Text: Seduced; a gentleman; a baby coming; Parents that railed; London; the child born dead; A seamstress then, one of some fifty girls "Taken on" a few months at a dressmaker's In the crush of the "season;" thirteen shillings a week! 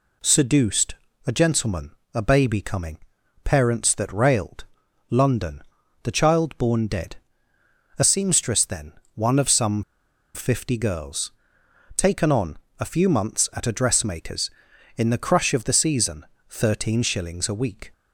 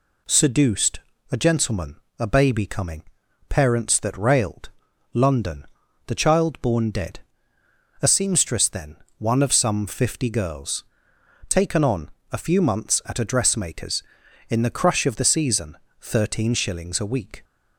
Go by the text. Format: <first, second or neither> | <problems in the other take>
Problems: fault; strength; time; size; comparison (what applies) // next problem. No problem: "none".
second | pauses between "some" and "fifty"; noticeable; at 9.8 s; 0.53 s long // pauses between "girls" and "Taken"; noticeable; at 11.3 s; 0.64 s long; noticeable in the second // pauses between "on" and "a"; slight; at 12.5 s; 0.22 s long; slight in the second